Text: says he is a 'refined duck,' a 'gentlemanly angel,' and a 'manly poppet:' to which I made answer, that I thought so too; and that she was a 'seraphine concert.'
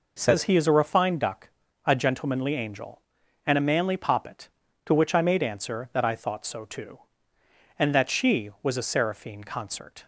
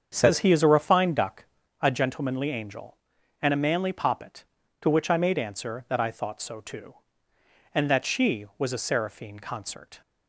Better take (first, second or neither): first